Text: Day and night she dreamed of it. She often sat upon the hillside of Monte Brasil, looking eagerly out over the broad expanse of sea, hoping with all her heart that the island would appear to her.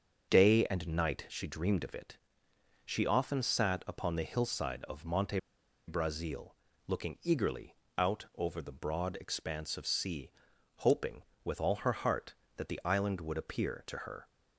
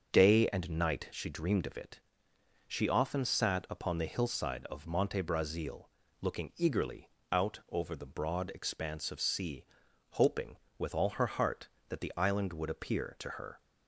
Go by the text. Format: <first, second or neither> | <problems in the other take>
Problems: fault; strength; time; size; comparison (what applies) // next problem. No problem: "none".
second | starts louder than the rest; until 1.3 s; 7 dB; also in the second // pauses between "Monte" and "Brasil"; noticeable; at 5.3 s; 0.47 s long // pauses between "eagerly" and "out"; slight; at 7.7 s; 0.22 s long; slight in the second